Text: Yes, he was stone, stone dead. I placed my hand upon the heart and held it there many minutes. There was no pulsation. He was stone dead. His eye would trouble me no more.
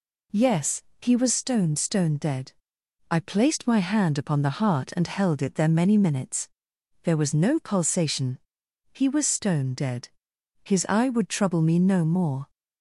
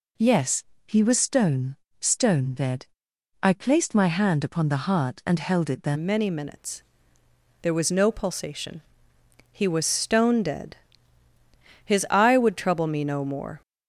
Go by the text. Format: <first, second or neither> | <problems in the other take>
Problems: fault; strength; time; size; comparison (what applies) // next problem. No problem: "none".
first | changes voice at "many"; from 5.9 s on; 7.7 s long